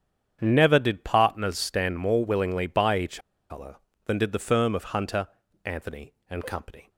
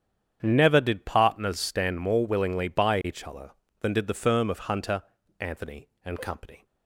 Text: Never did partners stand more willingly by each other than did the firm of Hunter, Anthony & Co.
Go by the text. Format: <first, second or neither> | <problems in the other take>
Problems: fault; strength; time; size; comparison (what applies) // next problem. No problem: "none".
second | starts louder than the rest; strong; until 1.4 s; 8.5 dB; strong in the second // pauses between "each" and "other"; slight; at 3.2 s; 0.30 s long